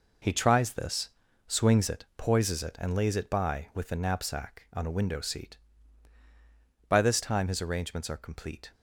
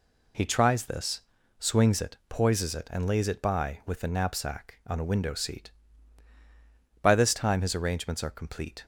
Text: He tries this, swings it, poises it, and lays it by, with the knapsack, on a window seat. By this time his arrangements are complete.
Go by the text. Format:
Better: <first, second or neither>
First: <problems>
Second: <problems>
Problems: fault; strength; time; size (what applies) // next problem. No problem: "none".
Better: second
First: gets quieter; strong; throughout; 9 dB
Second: none